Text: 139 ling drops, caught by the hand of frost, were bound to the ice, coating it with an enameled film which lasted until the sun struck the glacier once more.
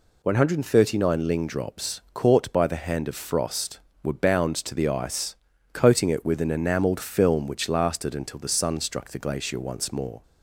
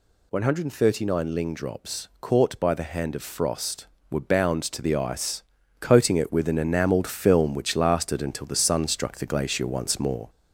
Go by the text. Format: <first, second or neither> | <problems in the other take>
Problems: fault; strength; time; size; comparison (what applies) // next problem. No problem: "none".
first | gets louder; slight; throughout; 2 dB